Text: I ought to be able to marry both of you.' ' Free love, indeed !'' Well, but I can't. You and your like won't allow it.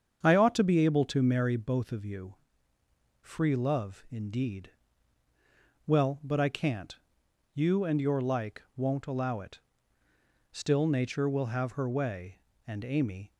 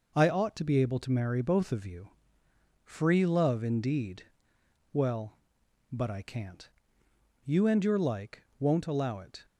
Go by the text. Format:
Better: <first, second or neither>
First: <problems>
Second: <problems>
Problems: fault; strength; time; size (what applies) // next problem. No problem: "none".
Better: second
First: starts louder than the rest; strong; until 1.2 s; 7.5 dB // pauses between "like" and "won't"; slight; at 8.6 s; 0.16 s long // goes on to say "Still Nature will have her way and Amy"; strong; from 10.5 s on; 2.8 s long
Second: pauses between "like" and "won't"; slight; at 8.4 s; 0.16 s long